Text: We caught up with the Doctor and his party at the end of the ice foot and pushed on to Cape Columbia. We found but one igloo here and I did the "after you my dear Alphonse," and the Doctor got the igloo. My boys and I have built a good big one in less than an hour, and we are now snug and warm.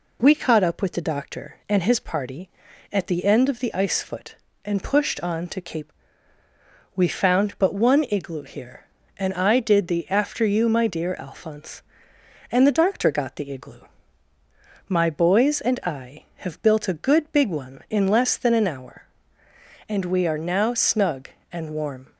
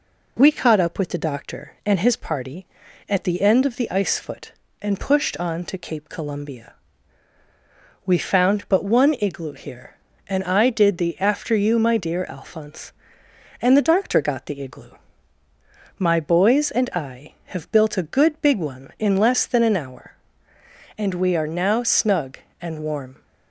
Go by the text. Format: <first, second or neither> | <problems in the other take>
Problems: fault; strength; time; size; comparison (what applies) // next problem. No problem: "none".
second | skips "Columbia"; at 6.4 s